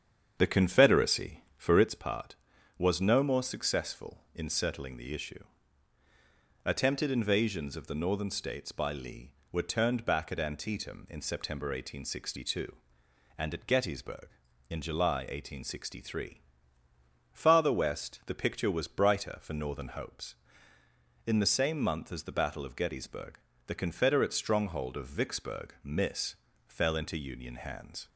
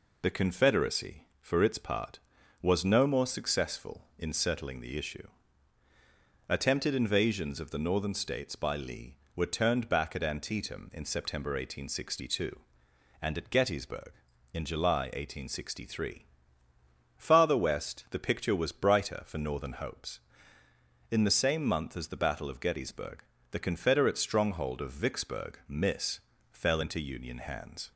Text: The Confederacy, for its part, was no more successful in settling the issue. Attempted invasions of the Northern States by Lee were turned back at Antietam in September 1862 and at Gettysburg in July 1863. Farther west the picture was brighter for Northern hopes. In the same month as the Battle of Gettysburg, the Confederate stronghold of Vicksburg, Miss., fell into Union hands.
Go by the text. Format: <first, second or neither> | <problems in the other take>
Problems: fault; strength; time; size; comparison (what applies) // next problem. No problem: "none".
second | starts louder than the rest; strong; until 1.9 s; 8 dB